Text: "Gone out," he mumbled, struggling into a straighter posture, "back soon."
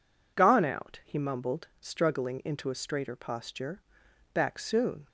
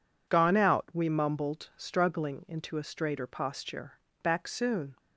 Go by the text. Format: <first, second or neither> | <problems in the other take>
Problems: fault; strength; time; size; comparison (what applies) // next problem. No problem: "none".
first | says "we" for "he"; at 0.9 s